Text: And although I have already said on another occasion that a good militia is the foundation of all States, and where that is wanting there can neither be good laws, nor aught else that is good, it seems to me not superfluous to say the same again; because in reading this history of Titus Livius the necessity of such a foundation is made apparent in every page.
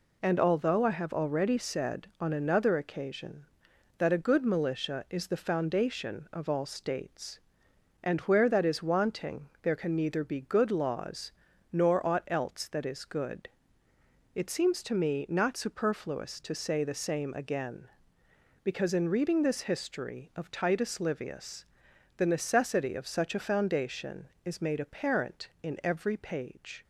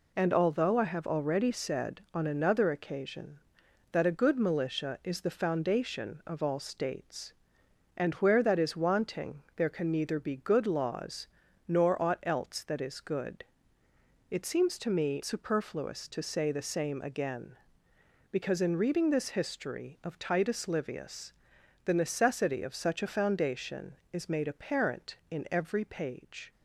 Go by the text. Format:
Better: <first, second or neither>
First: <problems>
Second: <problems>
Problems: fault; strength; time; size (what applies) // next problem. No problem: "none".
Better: first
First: pauses between "Livius" and "the"; noticeable; at 21.6 s; 0.54 s long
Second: skips "not"; at 15.2 s // pauses between "Livius" and "the"; noticeable; at 21.3 s; 0.54 s long